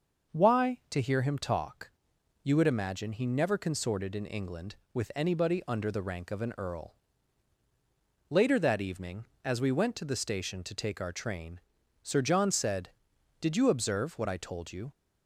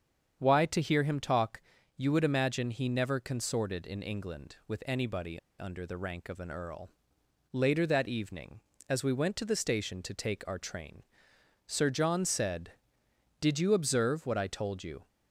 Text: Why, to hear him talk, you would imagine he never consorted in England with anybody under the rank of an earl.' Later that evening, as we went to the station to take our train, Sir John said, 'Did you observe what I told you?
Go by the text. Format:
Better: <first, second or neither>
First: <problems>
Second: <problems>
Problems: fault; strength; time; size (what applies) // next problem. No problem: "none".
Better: first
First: starts louder than the rest; until 1.4 s; 6 dB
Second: starts louder than the rest; strong; until 1.4 s; 7.5 dB // pauses between "anybody" and "under"; slight; at 5.3 s; 0.19 s long